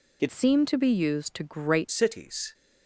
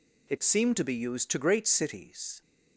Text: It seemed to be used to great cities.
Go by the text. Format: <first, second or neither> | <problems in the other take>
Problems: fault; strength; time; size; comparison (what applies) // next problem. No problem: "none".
second | changes voice from "seemed" to "great"; from 0.3 to 1.8 s; 1.5 s long